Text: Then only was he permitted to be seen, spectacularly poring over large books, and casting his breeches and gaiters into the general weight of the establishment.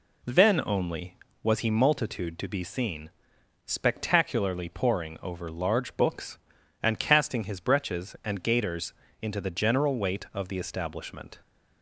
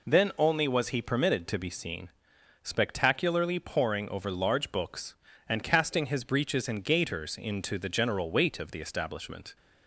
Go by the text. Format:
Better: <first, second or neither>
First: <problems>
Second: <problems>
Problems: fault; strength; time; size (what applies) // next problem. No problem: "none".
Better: second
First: says "multitude" for "permitted"; at 1.7 s // pauses between "gaiters" and "into"; slight; at 8.9 s; 0.28 s long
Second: none